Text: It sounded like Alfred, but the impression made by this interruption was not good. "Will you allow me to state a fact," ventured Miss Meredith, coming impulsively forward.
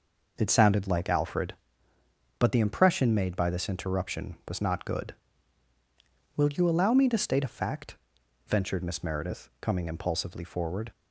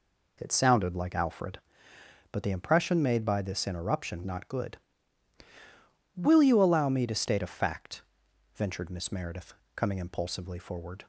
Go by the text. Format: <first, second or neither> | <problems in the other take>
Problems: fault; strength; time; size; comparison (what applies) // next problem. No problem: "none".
first | skips "was"; at 4.2 s